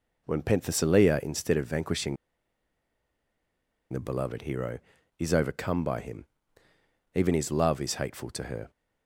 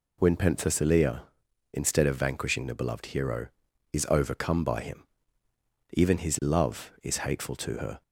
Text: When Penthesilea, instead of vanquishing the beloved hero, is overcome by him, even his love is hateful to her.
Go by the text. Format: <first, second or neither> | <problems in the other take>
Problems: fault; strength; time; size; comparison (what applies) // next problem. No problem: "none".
second | pauses between "vanquishing" and "the"; strong; at 2.1 s; 1.7 s long